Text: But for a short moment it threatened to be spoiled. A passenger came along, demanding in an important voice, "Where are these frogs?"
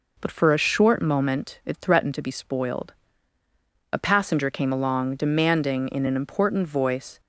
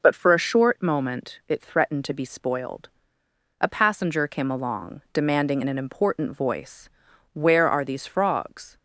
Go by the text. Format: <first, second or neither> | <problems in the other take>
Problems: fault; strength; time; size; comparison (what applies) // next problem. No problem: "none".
second | stops before "Where are these frogs"; at 7.1 s